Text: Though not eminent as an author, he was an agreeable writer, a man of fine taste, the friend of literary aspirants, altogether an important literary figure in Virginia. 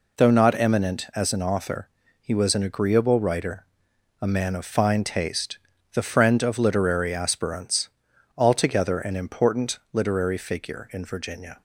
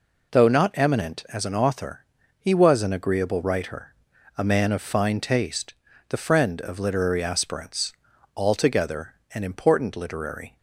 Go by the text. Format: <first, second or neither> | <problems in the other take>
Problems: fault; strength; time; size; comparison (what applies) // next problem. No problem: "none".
first | pauses between "altogether" and "an"; slight; at 9.1 s; 0.20 s long // stops before "figure in Virginia"; at 10.5 s